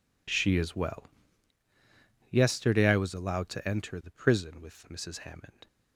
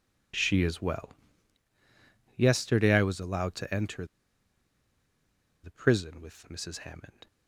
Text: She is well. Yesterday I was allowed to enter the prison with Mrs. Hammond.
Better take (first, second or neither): first